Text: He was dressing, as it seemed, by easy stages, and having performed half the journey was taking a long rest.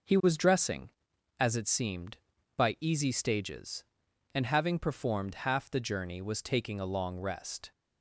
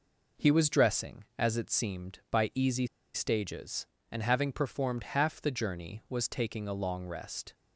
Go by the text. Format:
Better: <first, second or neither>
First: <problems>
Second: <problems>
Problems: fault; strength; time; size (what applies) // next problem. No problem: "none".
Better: first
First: none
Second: pauses between "easy" and "stages"; slight; at 2.8 s; 0.28 s long